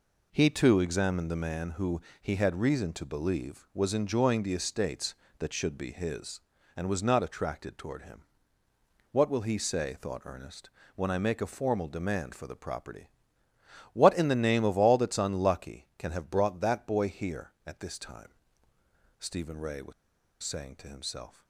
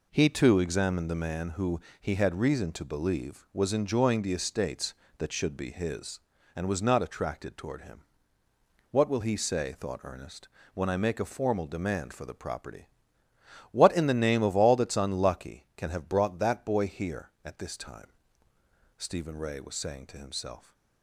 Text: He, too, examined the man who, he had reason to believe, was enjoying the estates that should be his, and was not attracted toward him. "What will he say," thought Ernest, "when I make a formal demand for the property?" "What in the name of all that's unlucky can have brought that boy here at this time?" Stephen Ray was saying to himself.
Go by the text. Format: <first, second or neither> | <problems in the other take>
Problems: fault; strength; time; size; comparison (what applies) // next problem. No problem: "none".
second | pauses between "was" and "saying"; noticeable; at 19.9 s; 0.50 s long